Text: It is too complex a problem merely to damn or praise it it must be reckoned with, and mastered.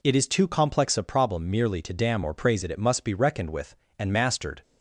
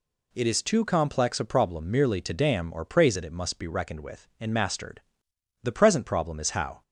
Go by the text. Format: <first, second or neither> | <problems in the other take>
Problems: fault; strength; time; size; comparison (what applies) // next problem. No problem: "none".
first | goes on to say "The present problem is how"; noticeable; from 5.6 s on; 1.1 s long